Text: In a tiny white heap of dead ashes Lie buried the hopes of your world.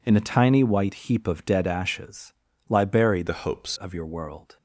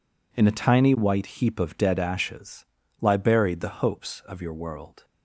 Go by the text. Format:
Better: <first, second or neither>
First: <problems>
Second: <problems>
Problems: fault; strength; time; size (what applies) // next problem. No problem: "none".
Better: second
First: pauses between "ashes" and "Lie"; at 2.3 s; 0.38 s long // changes voice from "the" to "hopes"; from 3.2 to 3.7 s; 0.5 s long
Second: pauses between "ashes" and "Lie"; at 2.6 s; 0.38 s long